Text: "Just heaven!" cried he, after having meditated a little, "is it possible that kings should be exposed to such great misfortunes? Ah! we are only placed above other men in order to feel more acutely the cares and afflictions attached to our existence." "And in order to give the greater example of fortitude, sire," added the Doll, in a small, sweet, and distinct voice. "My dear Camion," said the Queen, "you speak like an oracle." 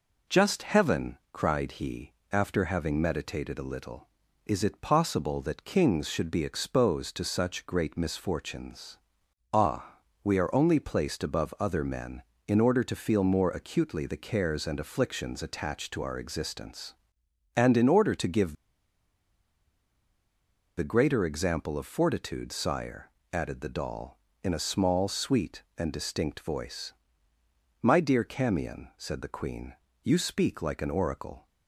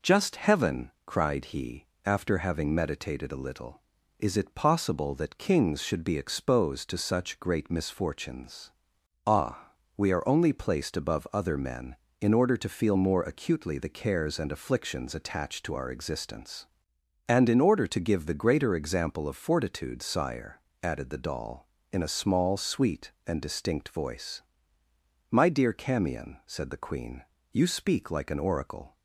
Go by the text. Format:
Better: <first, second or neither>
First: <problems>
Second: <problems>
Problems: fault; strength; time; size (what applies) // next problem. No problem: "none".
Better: second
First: pauses between "give" and "the"; strong; at 18.5 s; 2.2 s long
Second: none